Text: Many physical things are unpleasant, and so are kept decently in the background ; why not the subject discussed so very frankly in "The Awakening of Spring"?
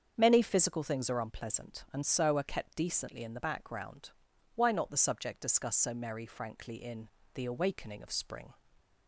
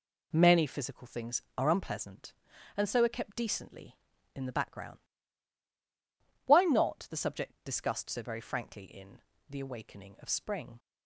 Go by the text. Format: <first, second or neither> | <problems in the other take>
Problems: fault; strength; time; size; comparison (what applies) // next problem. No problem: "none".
second | starts louder than the rest; strong; until 1.1 s; 7 dB // says "merry" for "very"; at 5.9 s // pauses between "in" and "The"; slight; at 7.0 s; 0.28 s long; slight in the second